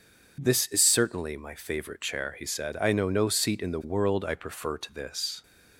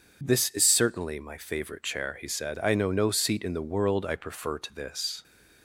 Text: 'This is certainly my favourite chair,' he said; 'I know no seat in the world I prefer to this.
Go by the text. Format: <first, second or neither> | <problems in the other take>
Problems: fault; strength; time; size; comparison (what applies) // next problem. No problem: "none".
neither | none